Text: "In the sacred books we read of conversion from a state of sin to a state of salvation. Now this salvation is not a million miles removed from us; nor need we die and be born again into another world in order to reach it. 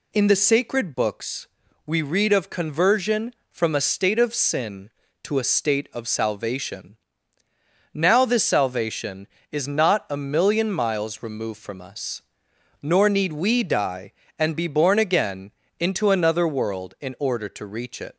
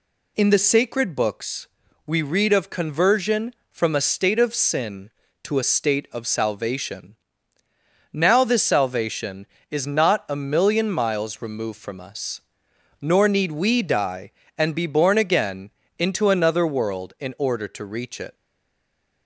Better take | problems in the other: first | pauses between "books" and "we"; at 1.6 s; 0.38 s long; also in the first // pauses between "again" and "into"; slight; at 15.6 s; 0.30 s long; slight in the first // stays silent after the last word; slight; from 18.3 s on; 0.9 s long

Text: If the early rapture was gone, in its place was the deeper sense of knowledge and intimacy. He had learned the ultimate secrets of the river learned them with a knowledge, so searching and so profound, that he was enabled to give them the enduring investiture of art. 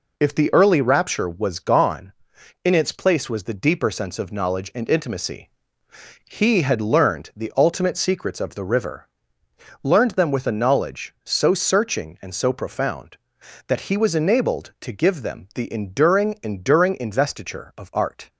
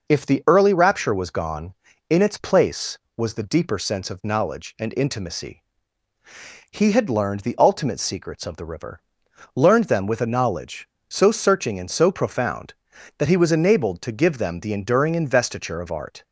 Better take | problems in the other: second | pauses between "river" and "learned"; noticeable; at 9.0 s; 0.76 s long; noticeable in the second // says "enduring" twice; at 16.4 s

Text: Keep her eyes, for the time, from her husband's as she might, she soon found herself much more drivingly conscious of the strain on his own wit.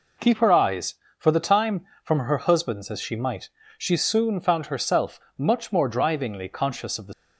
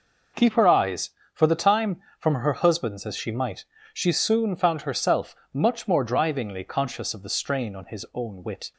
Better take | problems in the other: second | pauses between "herself" and "much"; slight; at 5.1 s; 0.18 s long; slight in the second // stops before "strain on his own wit"; at 7.1 s

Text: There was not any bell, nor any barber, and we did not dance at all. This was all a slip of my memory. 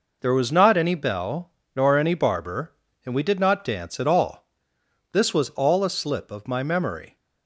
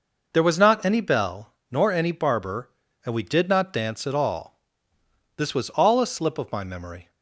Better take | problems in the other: neither | none

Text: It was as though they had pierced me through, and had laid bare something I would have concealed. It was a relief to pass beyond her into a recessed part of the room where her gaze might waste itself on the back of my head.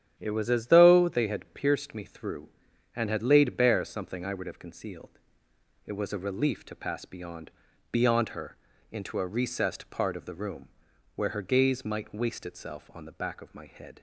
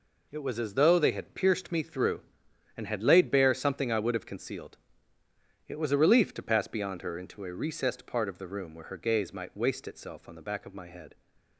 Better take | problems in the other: second | starts louder than the rest; strong; until 1.1 s; 9.5 dB // says "beyond" twice; at 7.9 s // pauses between "her" and "into"; slight; at 8.5 s; 0.34 s long // pauses between "room" and "where"; noticeable; at 10.6 s; 0.48 s long

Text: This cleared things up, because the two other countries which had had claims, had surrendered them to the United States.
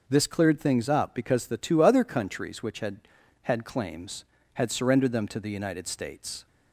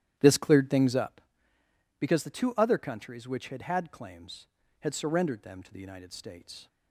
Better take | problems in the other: first | starts louder than the rest; strong; until 1.3 s; 11.5 dB

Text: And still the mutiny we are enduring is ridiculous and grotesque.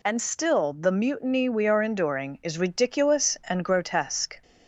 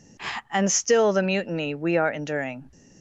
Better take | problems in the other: first | stops before "is ridiculous and grotesque"; at 2.7 s

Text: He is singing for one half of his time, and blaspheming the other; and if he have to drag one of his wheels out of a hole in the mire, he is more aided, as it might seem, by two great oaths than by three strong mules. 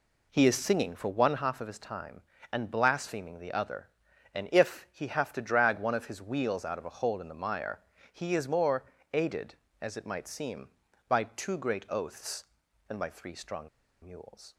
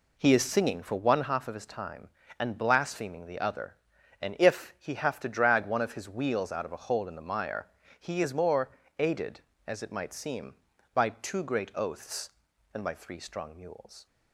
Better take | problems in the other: second | pauses between "more" and "aided"; slight; at 8.8 s; 0.28 s long; slight in the second // pauses between "strong" and "mules"; slight; at 13.6 s; 0.35 s long

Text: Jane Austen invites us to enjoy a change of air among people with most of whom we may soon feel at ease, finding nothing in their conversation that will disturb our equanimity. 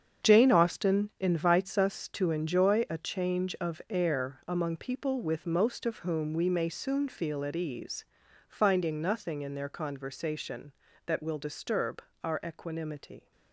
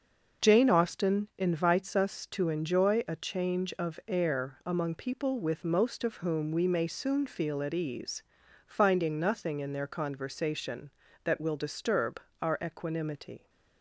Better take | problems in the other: second | gets quieter; strong; throughout; 11.5 dB // starts louder than the rest; strong; until 1.3 s; 8 dB; also in the second // pauses between "disturb" and "our"; slight; at 12.0 s; 0.20 s long; slight in the second

